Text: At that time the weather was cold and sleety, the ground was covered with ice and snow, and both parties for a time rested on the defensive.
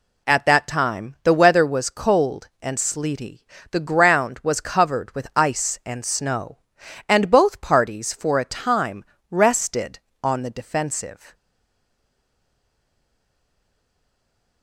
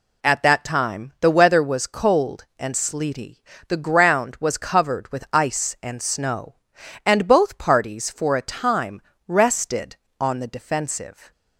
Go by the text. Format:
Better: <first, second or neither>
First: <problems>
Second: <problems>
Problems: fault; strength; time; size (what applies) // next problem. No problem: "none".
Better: second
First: pauses between "time" and "rested"; slight; at 9.0 s; 0.26 s long // stays silent after the last word; strong; from 11.3 s on; 3.3 s long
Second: pauses between "time" and "rested"; slight; at 9.0 s; 0.26 s long